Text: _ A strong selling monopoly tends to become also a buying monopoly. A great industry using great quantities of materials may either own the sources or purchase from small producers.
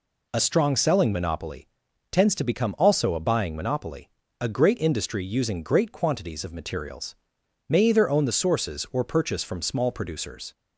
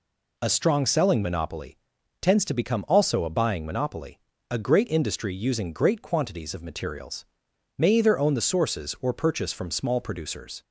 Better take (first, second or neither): neither